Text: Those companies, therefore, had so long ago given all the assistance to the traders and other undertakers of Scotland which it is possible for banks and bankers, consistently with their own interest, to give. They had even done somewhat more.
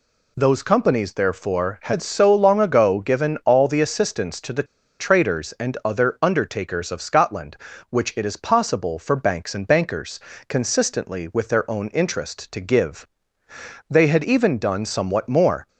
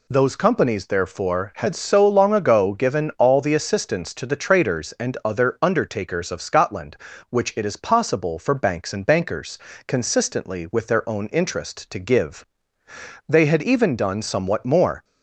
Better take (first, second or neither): second